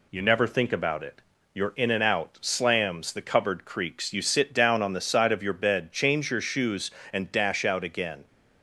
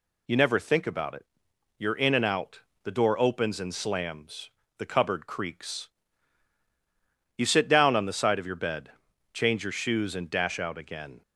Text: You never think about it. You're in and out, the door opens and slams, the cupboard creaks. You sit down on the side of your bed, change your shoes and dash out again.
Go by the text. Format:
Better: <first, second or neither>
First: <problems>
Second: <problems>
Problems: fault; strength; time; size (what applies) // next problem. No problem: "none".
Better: second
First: skips "the door opens and"; at 2.3 s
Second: none